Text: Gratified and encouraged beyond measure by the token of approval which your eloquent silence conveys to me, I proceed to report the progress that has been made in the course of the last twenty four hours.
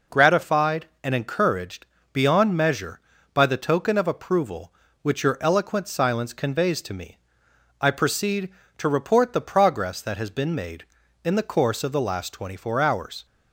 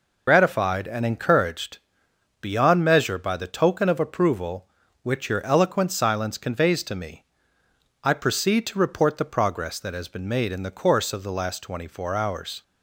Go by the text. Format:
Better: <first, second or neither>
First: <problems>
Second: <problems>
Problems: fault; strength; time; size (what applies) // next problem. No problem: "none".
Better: first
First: pauses between "encouraged" and "beyond"; slight; at 1.8 s; 0.28 s long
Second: loses the start of "Gratified"; at 0.2 s; 70 ms // pauses between "encouraged" and "beyond"; noticeable; at 1.7 s; 0.64 s long